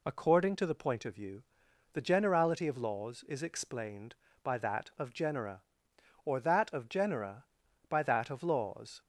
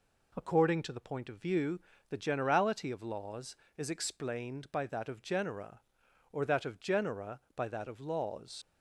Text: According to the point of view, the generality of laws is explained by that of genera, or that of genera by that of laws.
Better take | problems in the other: first | leaves "laws" unfinished; at 8.6 s; 55 ms

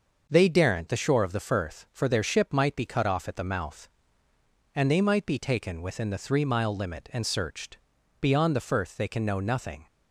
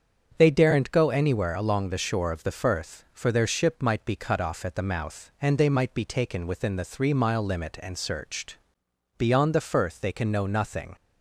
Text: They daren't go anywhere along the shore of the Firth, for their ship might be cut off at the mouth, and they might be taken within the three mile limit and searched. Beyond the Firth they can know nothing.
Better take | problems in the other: second | starts louder than the rest; noticeable; until 1.3 s; 6 dB; strong in the second // skips "go anywhere along"; at 0.8 s

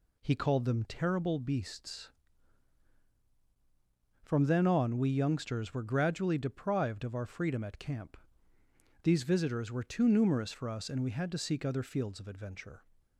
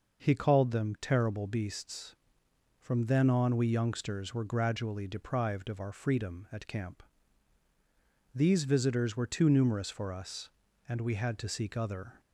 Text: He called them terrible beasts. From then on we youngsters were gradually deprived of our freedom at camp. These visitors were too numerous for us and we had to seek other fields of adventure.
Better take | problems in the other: first | stops before "fields of adventure"; at 12.2 s

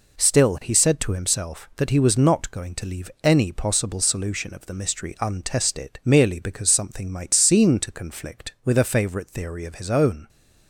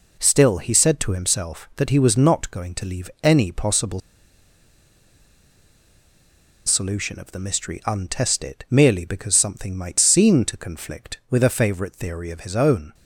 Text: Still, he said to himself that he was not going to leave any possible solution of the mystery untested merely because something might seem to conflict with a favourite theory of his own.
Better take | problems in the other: first | pauses between "possible" and "solution"; strong; at 3.9 s; 2.6 s long

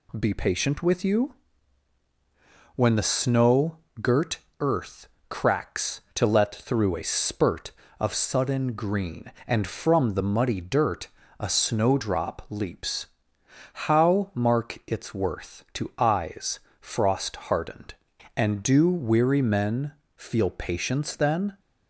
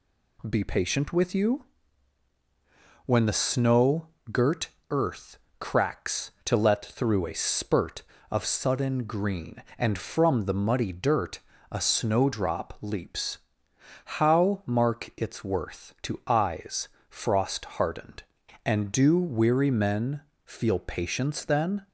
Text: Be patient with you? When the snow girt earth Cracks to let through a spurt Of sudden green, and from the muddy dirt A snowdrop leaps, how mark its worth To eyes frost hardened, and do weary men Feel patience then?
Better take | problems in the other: neither | pauses between "snow" and "girt"; slight; the same in both // pauses between "girt" and "earth"; slight; the same in both // pauses between "earth" and "Cracks"; slight; the same in both // pauses between "dirt" and "A"; slight; the same in both // pauses between "eyes" and "frost"; slight; the same in both // pauses between "men" and "Feel"; slight; the same in both

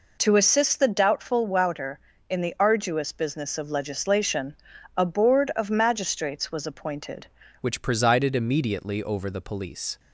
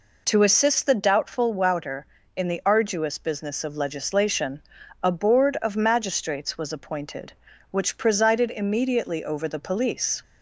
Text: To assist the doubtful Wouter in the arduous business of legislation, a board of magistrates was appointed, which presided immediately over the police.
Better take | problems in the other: second | changes voice at "which"; from 7.6 s on; 2.3 s long

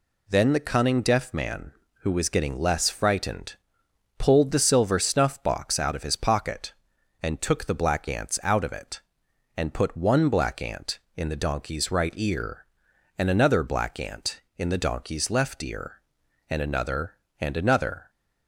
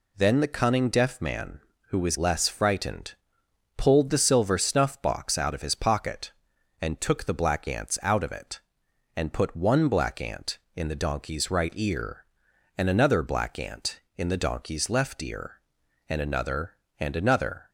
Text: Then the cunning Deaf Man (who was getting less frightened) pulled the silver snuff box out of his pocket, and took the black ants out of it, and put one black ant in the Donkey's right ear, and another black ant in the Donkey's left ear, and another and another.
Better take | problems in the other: first | skips "getting"; at 2.1 s

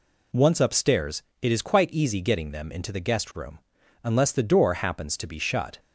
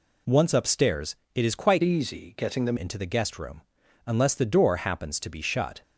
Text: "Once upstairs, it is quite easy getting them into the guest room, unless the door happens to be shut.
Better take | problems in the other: first | changes voice from "easy" to "them"; from 1.8 to 2.7 s; 0.9 s long

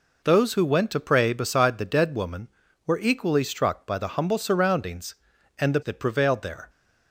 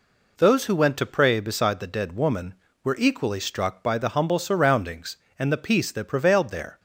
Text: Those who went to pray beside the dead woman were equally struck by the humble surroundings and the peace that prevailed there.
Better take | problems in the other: second | skips "peace"; at 5.8 s

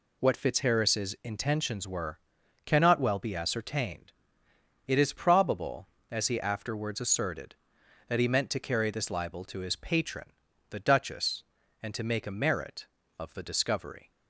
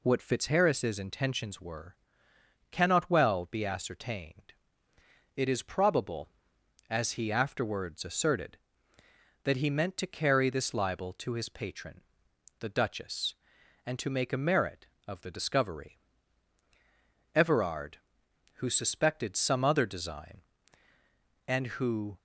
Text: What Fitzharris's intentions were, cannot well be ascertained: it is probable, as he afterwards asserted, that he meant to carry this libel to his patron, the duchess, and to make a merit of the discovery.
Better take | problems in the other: first | goes on to say "Everard who suspected some other design and who"; strong; from 17.3 s on; 4.8 s long

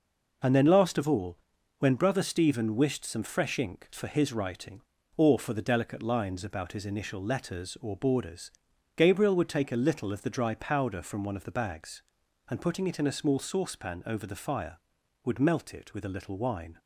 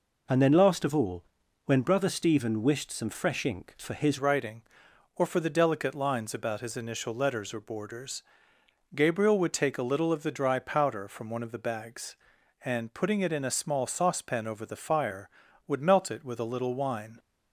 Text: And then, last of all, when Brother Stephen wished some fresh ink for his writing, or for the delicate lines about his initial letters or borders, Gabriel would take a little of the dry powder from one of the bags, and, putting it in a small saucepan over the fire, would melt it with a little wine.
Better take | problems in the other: first | changes voice at "writing"; from 4.1 s on; 13.0 s long

